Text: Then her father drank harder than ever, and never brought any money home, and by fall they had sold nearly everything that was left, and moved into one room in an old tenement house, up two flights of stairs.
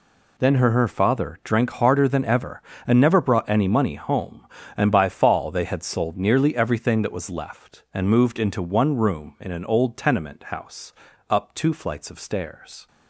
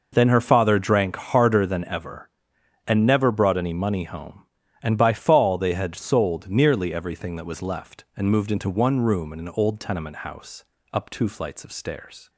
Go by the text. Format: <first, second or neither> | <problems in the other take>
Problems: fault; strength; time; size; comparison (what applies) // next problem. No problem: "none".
second | says "her" twice; at 0.7 s